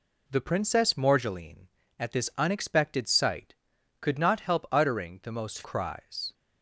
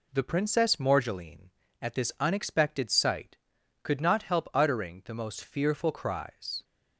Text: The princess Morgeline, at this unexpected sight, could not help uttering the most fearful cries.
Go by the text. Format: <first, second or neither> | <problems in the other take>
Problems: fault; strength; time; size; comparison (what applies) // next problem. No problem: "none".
second | skips "fearful"; at 5.6 s